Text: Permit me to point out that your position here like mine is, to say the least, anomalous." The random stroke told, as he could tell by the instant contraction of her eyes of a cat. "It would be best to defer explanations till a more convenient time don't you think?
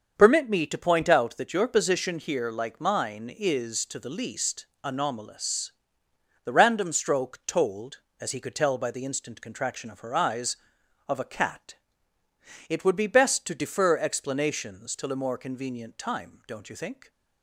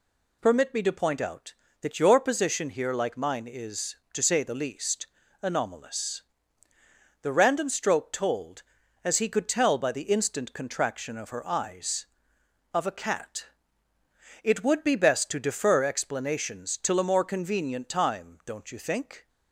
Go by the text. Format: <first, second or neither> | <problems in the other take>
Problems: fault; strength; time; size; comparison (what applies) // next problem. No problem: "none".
second | starts louder than the rest; until 1.1 s; 6.5 dB // skips "say"; at 3.9 s